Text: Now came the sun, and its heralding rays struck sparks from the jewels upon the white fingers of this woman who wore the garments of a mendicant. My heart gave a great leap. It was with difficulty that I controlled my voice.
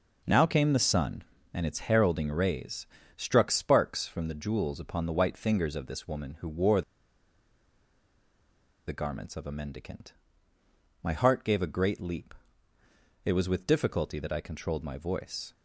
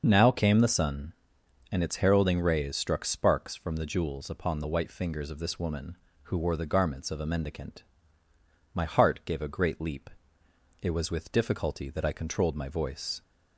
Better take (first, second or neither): second